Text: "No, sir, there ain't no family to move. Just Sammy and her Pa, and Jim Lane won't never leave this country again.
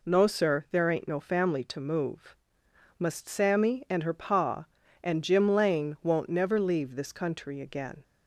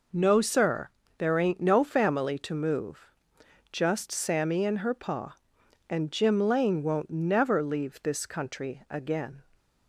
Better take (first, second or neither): second